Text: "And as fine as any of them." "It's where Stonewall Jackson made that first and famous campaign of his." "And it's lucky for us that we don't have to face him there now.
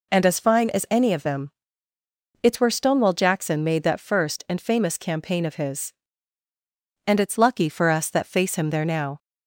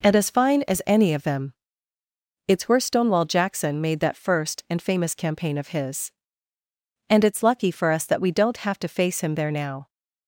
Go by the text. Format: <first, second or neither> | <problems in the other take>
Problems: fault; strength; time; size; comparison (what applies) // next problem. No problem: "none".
second | skips "we don't have to"; at 8.2 s